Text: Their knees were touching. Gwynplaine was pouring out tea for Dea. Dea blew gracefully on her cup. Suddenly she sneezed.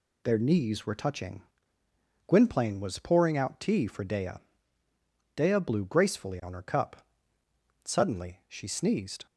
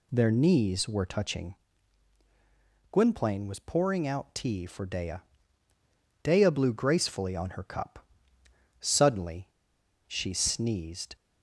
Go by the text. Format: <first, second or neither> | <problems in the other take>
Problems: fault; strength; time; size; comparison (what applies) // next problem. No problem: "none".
first | pauses between "Suddenly" and "she"; noticeable; at 9.4 s; 0.58 s long